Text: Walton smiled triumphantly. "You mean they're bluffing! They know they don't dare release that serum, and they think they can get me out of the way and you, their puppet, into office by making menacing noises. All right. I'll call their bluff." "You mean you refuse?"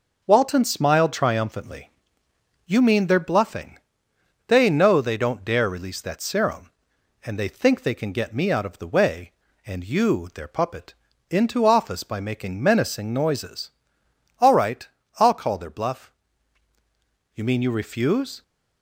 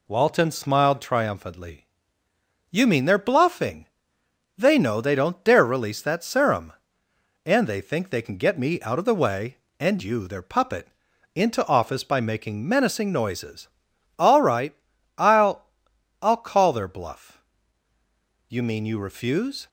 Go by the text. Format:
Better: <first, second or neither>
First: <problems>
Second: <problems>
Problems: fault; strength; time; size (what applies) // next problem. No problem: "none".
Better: first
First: none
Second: says "I'll" twice; at 16.2 s